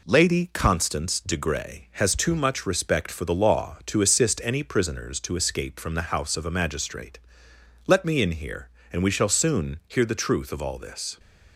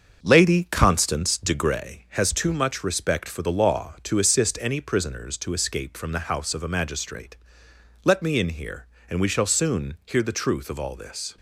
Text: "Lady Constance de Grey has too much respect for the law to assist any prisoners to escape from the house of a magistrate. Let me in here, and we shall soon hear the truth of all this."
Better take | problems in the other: first | starts louder than the rest; until 2.0 s; 6.5 dB

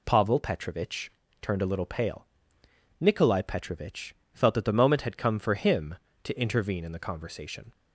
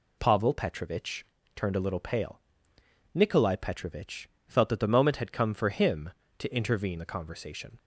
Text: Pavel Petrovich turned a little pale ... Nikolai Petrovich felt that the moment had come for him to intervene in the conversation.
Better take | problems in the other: first | pauses between "Petrovich" and "turned"; slight; at 1.2 s; 0.30 s long; slight in the first // pauses between "Petrovich" and "felt"; slight; at 4.2 s; 0.20 s long; slight in the first // skips "in"; at 6.9 s

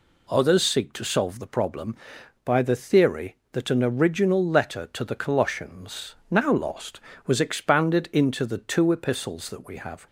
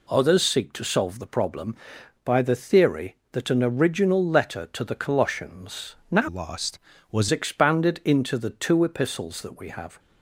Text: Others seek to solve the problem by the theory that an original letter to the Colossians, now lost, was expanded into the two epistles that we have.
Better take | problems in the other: first | changes voice from "lost" to "was"; from 6.2 to 7.2 s; 1.0 s long

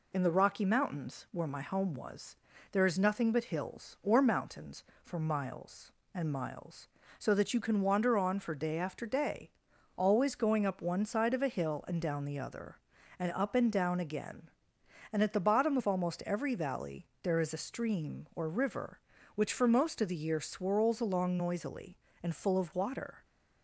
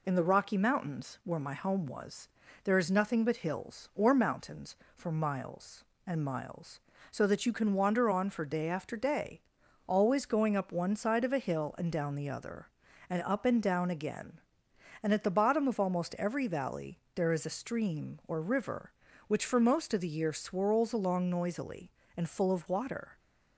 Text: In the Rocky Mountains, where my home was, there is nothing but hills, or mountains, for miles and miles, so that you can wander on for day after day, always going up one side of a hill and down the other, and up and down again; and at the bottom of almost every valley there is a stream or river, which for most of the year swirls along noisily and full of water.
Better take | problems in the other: neither | pauses between "valley" and "there"; slight; the same in both

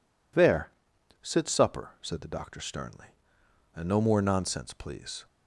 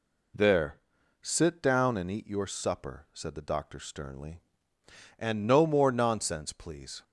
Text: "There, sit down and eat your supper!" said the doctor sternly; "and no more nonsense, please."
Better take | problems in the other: second | skips "down and eat your"; at 1.4 s

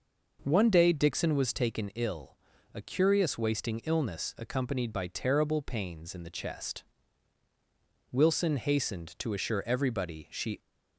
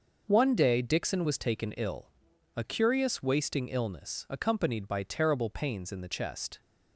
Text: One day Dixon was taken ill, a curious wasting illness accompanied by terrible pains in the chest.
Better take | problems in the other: second | goes on to say "Wilson hastened to assure everybody she"; strong; from 8.1 s on; 2.4 s long

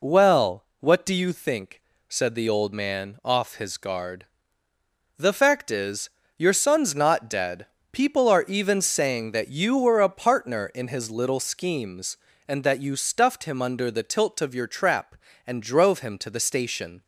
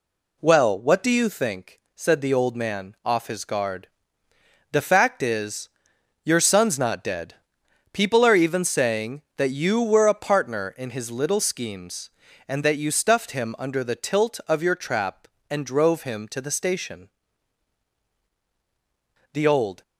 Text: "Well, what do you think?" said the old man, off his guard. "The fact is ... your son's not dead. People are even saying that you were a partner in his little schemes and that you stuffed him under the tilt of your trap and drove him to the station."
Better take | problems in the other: first | goes on to say "The old"; from 19.3 s on; 0.50 s long

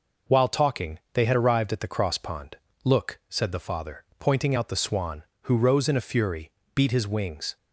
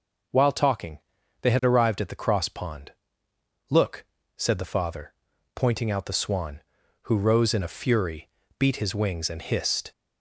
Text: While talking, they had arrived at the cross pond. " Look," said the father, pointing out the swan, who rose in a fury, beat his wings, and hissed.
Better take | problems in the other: second | stops before "and hissed"; at 7.5 s

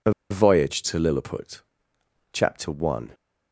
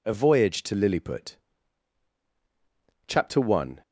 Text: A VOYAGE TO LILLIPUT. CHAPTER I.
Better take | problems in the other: second | pauses between "A" and "VOYAGE"; slight; at 0.1 s; 0.19 s long

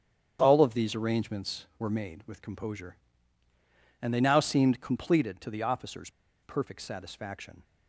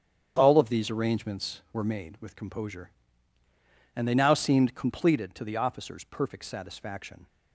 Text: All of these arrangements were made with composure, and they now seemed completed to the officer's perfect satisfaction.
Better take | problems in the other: second | starts louder than the rest; strong; until 1.4 s; 8.5 dB; strong in the second // pauses between "officer's" and "perfect"; slight; at 6.1 s; 0.31 s long

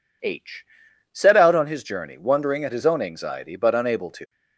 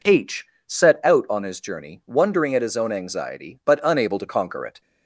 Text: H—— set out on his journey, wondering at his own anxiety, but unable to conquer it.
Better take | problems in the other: second | stops before "conquer it"; at 4.2 s

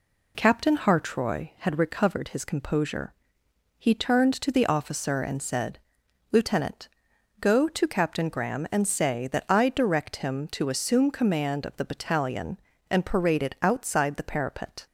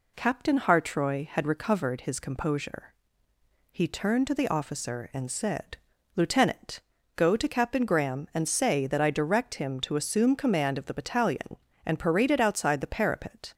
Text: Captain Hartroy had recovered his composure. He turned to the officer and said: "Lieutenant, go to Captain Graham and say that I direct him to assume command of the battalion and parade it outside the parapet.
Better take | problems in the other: neither | none

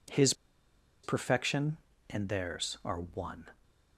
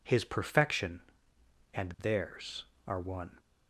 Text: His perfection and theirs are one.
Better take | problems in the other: second | pauses between "His" and "perfection"; noticeable; at 0.3 s; 0.70 s long

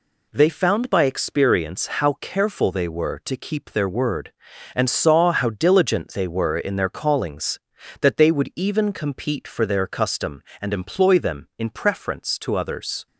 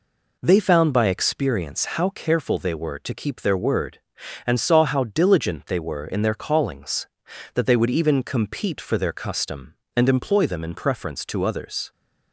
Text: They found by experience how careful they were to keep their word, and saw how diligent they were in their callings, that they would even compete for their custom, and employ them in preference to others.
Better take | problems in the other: neither | none

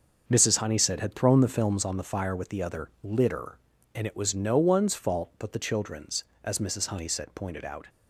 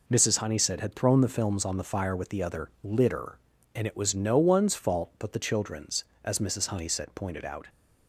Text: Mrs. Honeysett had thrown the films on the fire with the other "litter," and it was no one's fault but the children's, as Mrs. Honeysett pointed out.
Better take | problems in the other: second | starts louder than the rest; noticeable; until 1.9 s; 6 dB

